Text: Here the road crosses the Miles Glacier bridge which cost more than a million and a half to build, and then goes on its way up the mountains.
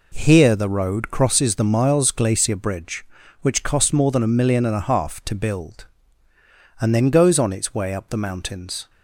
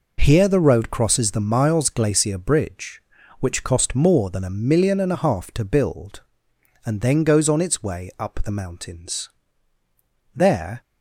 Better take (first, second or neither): first